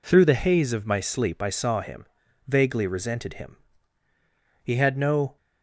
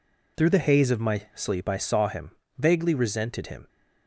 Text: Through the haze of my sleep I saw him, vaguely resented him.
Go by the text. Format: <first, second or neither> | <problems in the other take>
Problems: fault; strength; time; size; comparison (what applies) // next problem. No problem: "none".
second | goes on to say "He had no"; noticeable; from 4.6 s on; 0.74 s long